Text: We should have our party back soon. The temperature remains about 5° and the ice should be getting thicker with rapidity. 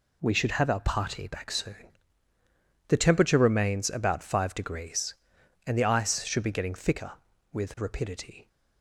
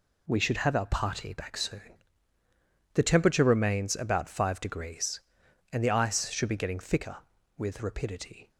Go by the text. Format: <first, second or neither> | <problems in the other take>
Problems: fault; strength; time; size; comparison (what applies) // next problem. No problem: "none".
neither | none